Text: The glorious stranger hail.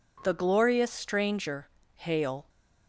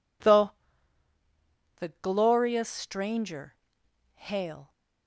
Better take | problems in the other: first | says "The" twice; at 1.7 s // pauses between "stranger" and "hail"; noticeable; at 3.5 s; 0.58 s long; slight in the first

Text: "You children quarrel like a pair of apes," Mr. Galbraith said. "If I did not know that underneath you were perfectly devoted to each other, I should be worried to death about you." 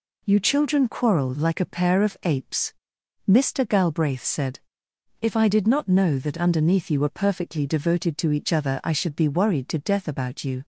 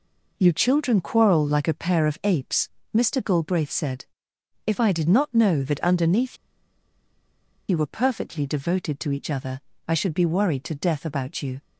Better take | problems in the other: first | pauses between "underneath" and "you"; strong; at 6.3 s; 1.3 s long

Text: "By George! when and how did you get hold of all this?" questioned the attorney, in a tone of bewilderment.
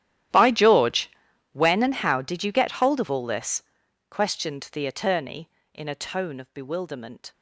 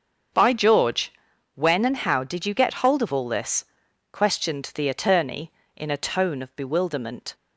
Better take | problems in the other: second | gets quieter; strong; throughout; 22 dB // starts louder than the rest; strong; until 1.7 s; 12 dB; also in the second

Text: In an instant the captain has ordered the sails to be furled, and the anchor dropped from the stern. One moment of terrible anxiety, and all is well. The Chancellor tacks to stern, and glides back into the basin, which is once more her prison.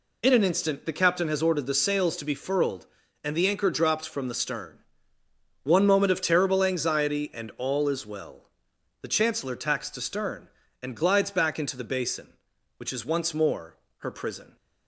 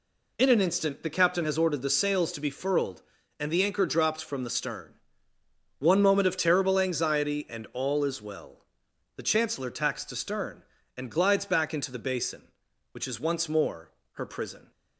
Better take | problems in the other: neither | pauses between "more" and "her"; slight; the same in both

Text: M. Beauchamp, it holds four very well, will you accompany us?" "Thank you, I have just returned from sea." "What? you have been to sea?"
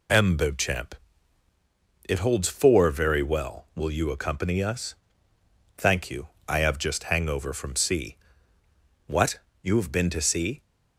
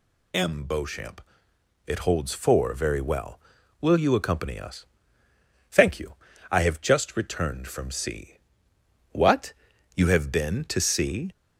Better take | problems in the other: second | says "hangover" for "returned"; at 7.0 s

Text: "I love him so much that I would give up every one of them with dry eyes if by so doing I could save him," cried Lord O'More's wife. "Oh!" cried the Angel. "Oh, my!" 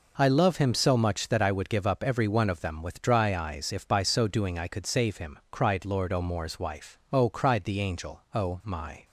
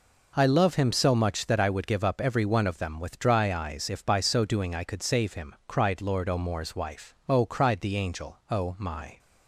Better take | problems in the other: neither | none

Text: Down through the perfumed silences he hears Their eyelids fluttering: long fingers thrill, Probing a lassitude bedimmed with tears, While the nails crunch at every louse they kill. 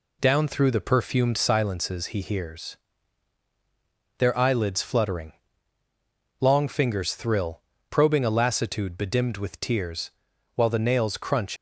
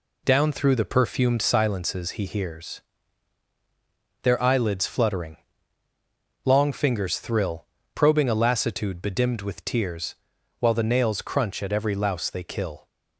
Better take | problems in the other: second | pauses between "hears" and "Their"; strong; at 2.7 s; 1.4 s long; strong in the second // stops before "at every louse they kill"; at 11.5 s

